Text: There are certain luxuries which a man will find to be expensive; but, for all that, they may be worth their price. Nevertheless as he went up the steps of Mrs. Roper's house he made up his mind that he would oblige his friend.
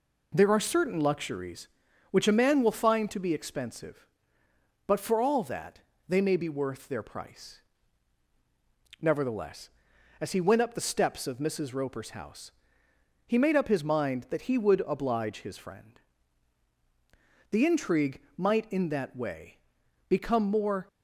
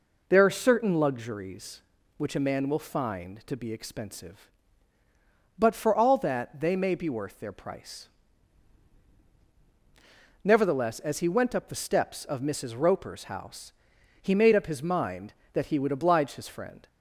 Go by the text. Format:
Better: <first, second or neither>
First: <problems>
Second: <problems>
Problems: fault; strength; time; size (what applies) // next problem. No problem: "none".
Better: second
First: pauses between "house" and "he"; noticeable; at 12.4 s; 0.76 s long // goes on to say "The intrigue might in that way become more"; strong; from 17.4 s on; 3.3 s long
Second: pauses between "house" and "he"; noticeable; at 13.7 s; 0.48 s long